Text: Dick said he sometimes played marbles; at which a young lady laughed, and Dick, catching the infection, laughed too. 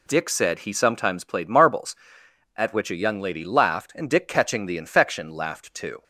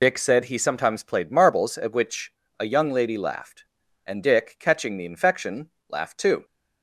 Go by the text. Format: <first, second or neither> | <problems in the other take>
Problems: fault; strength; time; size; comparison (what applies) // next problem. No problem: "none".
first | loses the start of "Dick"; at 0.0 s; 55 ms // pauses between "which" and "a"; slight; at 2.3 s; 0.28 s long